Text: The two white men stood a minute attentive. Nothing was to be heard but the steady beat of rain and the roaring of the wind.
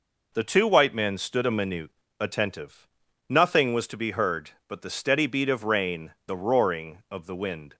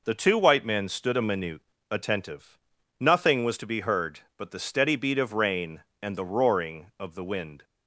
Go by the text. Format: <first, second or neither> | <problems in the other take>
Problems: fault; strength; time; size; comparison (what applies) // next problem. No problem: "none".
second | pauses between "minute" and "attentive"; slight; at 1.8 s; 0.32 s long; slight in the second // skips "and"; at 6.2 s